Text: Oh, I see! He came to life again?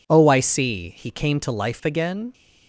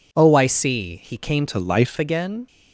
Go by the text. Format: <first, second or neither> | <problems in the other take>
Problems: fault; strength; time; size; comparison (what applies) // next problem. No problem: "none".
first | changes voice from "to" to "life"; from 1.4 to 1.9 s; 0.5 s long